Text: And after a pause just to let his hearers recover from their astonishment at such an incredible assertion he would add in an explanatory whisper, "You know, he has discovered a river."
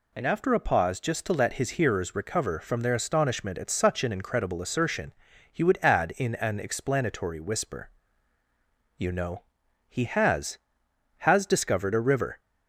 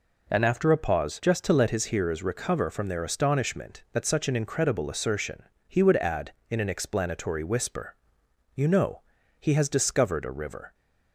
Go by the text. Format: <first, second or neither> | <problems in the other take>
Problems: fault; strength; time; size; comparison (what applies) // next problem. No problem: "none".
second | pauses between "assertion" and "he"; at 5.1 s; 0.38 s long; slight in the second // says "has" twice; at 11.1 s